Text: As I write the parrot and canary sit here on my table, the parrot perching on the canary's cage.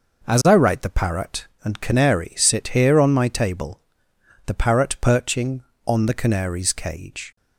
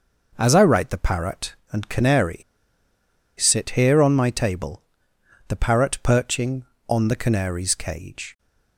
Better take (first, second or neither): first